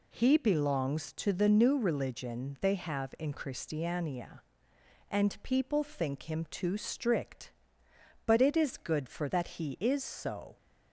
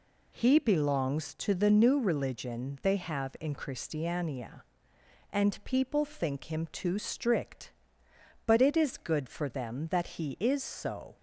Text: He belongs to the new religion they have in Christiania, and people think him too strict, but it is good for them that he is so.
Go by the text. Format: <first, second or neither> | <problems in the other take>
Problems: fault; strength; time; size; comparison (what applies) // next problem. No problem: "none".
second | skips "them"; at 9.2 s